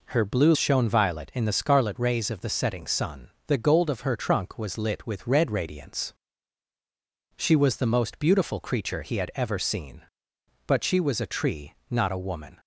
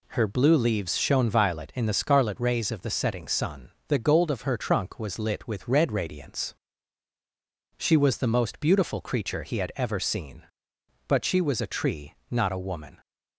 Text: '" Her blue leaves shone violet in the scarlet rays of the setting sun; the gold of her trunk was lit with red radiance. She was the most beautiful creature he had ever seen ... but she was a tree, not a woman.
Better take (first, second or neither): second